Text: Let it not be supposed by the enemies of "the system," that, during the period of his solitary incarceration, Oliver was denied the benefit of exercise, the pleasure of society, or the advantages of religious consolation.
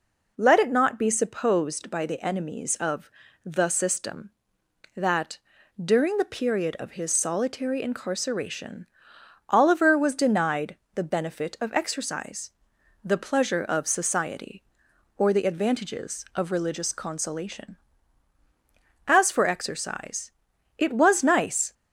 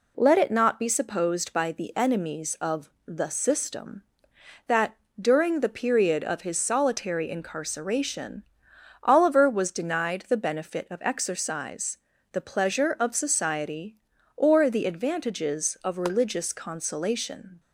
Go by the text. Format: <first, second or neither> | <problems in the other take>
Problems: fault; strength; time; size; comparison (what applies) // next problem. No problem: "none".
second | pauses between "of" and "the"; slight; at 3.1 s; 0.34 s long; slight in the second // pauses between "denied" and "the"; slight; at 10.7 s; 0.20 s long // goes on to say "As for exercise it was nice"; strong; from 19.0 s on; 2.6 s long